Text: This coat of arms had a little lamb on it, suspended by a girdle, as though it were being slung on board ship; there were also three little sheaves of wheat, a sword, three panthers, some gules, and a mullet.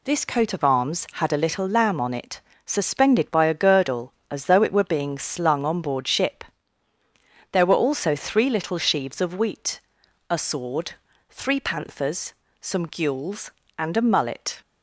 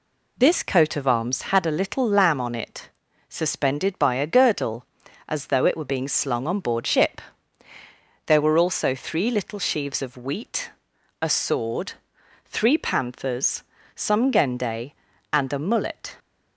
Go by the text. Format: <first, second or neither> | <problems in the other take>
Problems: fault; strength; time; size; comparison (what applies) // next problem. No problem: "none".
first | says "gende" for "gules"; at 14.3 s